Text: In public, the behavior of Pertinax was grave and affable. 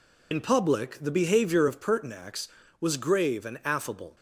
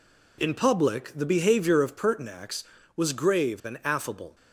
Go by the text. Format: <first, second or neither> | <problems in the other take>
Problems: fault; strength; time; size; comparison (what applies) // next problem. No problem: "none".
second | loses the start of "In"; at 0.3 s; 65 ms